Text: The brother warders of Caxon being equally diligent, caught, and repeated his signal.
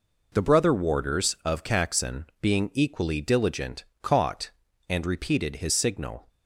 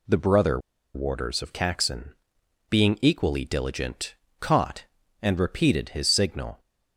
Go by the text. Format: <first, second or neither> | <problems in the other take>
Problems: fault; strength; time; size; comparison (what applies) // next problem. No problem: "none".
first | pauses between "brother" and "warders"; at 0.5 s; 0.36 s long // pauses between "Caxon" and "being"; noticeable; at 2.1 s; 0.56 s long; slight in the first